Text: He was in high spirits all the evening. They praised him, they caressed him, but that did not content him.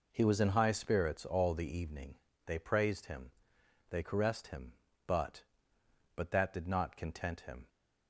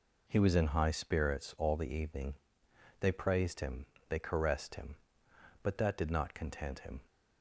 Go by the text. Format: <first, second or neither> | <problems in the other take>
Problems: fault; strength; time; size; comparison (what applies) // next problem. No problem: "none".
second | says "but" twice; at 6.1 s